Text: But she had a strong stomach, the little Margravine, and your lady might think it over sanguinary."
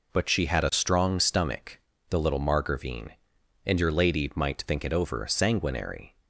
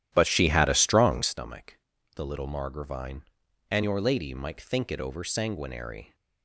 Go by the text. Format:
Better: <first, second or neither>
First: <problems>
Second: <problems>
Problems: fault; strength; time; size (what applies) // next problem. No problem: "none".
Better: first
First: none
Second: starts louder than the rest; strong; until 1.3 s; 11.5 dB